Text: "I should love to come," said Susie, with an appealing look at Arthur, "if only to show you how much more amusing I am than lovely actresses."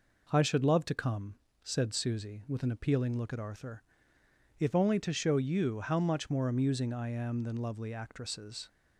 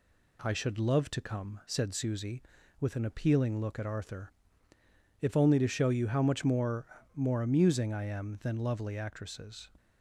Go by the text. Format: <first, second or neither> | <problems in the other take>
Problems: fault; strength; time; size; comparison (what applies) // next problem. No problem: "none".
first | says "more" twice; at 7.1 s